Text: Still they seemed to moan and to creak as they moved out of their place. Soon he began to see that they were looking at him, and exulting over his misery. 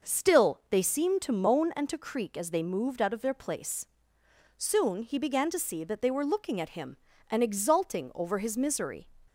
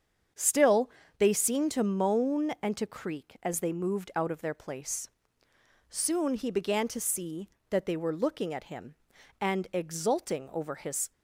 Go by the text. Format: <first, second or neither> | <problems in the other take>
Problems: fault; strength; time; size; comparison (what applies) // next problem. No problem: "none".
first | starts louder than the rest; strong; until 1.6 s; 7 dB // pauses between "Still" and "they"; slight; at 0.8 s; 0.28 s long // stops before "misery"; at 11.1 s